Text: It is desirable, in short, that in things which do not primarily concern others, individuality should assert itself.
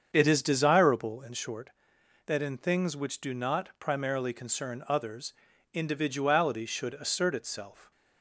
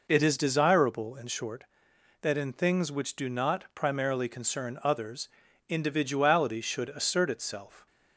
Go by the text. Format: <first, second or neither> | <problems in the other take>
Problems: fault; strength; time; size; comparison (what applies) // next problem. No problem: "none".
second | starts louder than the rest; strong; until 1.2 s; 7.5 dB